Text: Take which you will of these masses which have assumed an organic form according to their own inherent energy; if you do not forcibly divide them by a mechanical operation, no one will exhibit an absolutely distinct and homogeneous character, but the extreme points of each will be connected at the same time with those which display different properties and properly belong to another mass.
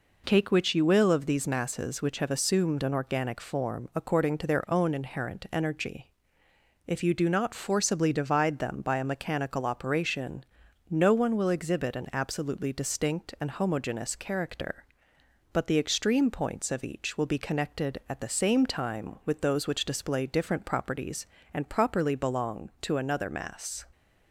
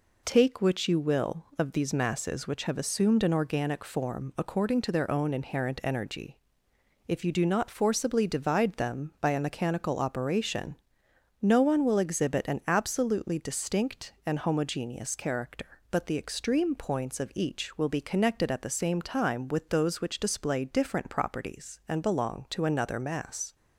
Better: first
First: none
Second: skips "properly"; at 22.0 s

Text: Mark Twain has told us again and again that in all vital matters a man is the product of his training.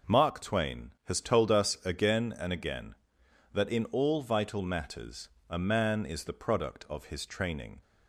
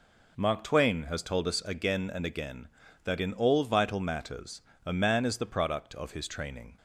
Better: neither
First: pauses between "matters" and "a"; slight; at 5.2 s; 0.20 s long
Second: pauses between "matters" and "a"; slight; at 4.6 s; 0.24 s long

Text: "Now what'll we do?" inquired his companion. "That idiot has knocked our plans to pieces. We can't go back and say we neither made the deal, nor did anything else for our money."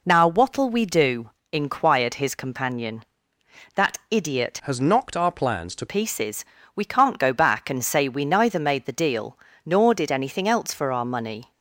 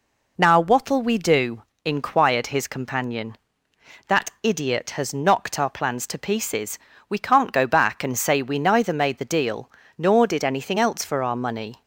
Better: second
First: changes voice from "has" to "to"; from 4.6 to 5.8 s; 1.2 s long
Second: none

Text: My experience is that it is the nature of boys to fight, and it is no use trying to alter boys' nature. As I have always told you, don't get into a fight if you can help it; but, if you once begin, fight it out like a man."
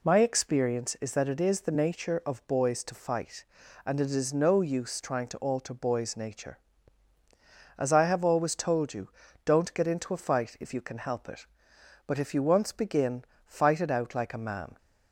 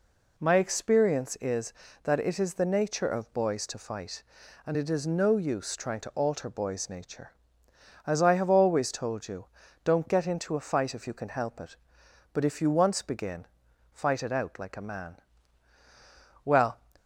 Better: first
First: none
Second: goes on to say "Well"; slight; from 16.4 s on; 0.36 s long

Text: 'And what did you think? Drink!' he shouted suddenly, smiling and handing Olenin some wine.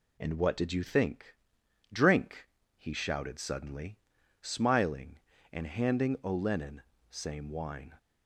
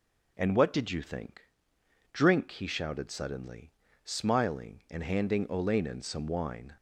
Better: second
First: says "same" for "some"; at 7.0 s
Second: none

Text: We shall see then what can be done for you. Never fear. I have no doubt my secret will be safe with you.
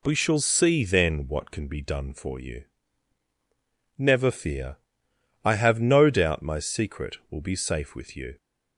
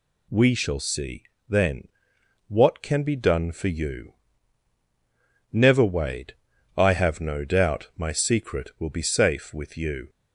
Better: first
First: none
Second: pauses between "see" and "then"; slight; at 1.2 s; 0.24 s long // pauses between "then" and "what"; noticeable; at 1.8 s; 0.60 s long // says "wade" for "fear"; at 5.8 s

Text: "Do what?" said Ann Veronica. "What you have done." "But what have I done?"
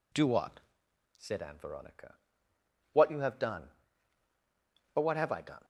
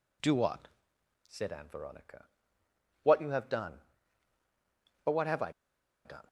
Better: first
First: none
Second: pauses between "I" and "done"; noticeable; at 5.5 s; 0.54 s long

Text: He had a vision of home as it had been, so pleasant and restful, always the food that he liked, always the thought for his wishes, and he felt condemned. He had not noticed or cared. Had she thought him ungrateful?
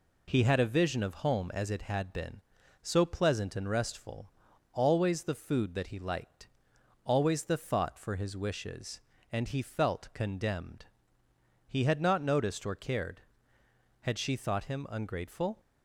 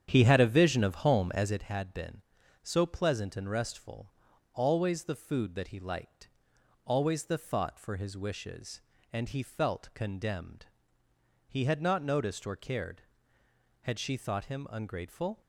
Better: first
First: none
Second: starts louder than the rest; strong; until 1.7 s; 9 dB

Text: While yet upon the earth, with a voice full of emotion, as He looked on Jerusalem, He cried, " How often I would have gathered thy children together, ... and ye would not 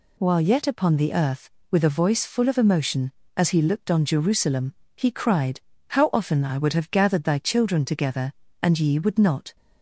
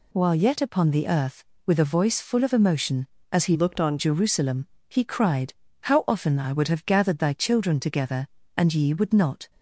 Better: first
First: none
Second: changes voice from "looked" to "on"; from 3.5 to 3.9 s; 0.4 s long

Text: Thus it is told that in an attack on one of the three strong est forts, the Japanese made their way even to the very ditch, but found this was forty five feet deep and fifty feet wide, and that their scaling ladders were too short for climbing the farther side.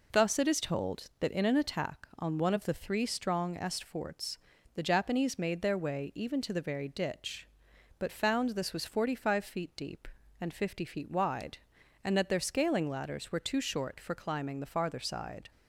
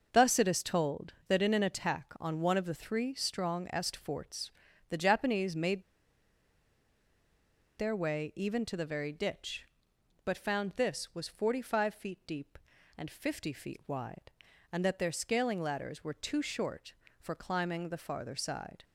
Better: first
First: none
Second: starts louder than the rest; until 1.1 s; 6 dB // pauses between "made" and "their"; strong; at 5.8 s; 1.9 s long

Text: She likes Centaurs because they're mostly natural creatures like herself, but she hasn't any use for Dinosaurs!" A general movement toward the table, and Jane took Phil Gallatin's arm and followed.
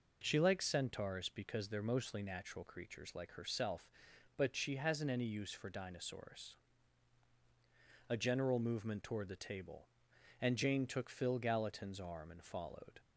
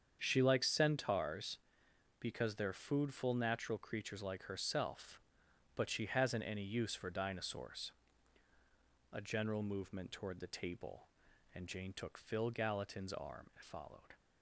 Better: first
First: none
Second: starts louder than the rest; strong; until 1.2 s; 7.5 dB // says "foodful" for "mostly"; at 2.7 s

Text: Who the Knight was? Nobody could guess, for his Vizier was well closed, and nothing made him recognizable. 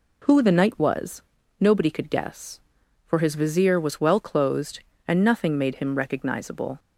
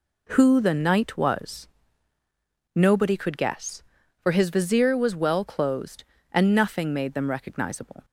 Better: first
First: none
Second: says "them" for "him"; at 7.1 s

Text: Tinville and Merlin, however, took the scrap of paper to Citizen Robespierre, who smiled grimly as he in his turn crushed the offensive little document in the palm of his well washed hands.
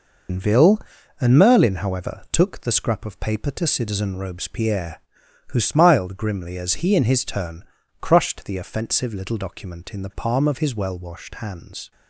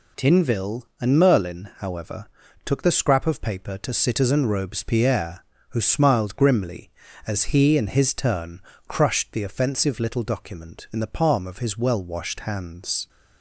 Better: second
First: loses the start of "Tinville"; at 0.2 s; 160 ms // pauses between "turn" and "crushed"; at 7.6 s; 0.38 s long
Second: pauses between "turn" and "crushed"; slight; at 8.6 s; 0.28 s long

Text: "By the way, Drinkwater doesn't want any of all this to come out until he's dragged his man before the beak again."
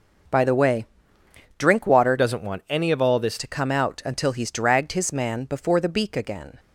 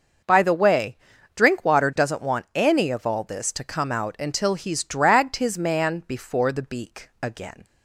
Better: second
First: changes voice from "doesn't" to "this"; from 2.1 to 3.3 s; 1.2 s long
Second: none

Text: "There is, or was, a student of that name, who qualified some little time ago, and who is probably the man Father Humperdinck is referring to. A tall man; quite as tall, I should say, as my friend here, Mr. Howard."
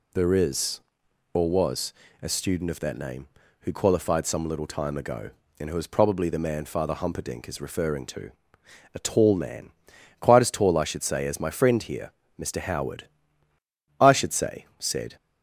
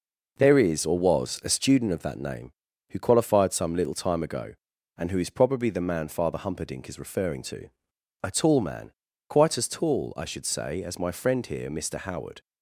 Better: second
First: goes on to say "I should say said"; noticeable; from 13.9 s on; 1.1 s long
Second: none

